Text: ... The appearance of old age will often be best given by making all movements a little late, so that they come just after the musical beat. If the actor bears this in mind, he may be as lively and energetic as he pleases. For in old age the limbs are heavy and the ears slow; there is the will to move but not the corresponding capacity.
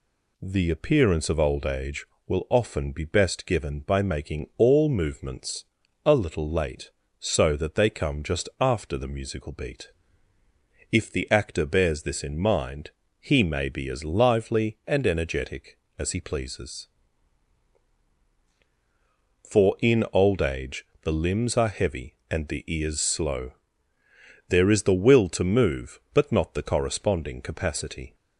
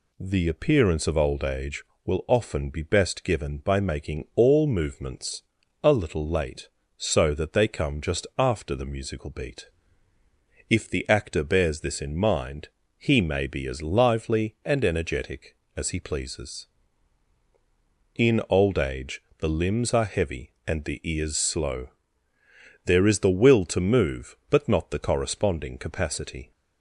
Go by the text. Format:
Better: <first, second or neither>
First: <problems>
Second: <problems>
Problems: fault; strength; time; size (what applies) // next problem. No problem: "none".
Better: first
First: pauses between "movements" and "a"; at 5.6 s; 0.40 s long // pauses between "age" and "the"; slight; at 20.8 s; 0.18 s long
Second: pauses between "movements" and "a"; at 5.4 s; 0.40 s long // skips "For"; at 17.4 s // pauses between "age" and "the"; slight; at 19.2 s; 0.18 s long